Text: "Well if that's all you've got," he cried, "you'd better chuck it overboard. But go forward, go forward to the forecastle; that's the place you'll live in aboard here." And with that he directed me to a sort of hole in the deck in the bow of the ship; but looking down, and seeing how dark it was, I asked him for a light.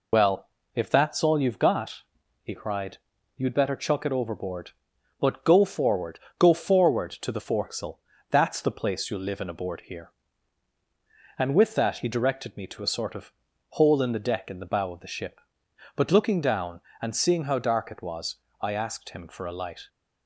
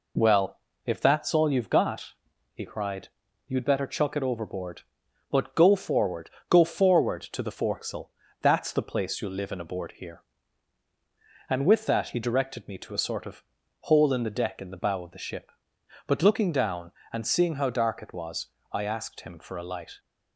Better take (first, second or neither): second